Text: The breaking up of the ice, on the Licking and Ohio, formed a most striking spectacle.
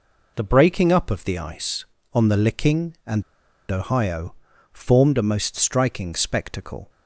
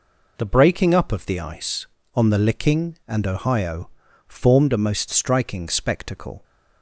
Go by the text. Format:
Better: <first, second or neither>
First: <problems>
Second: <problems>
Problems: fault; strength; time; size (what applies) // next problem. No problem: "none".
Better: second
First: pauses between "and" and "Ohio"; noticeable; at 3.2 s; 0.49 s long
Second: none